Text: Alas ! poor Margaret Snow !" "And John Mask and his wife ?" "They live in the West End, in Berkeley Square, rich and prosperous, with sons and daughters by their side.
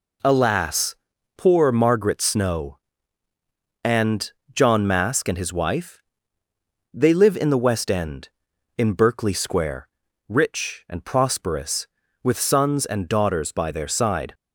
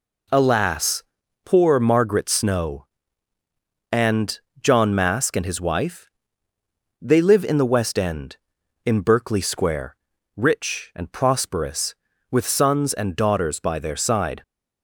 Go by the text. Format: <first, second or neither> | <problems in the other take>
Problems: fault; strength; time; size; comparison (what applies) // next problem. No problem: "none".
neither | pauses between "And" and "John"; slight; the same in both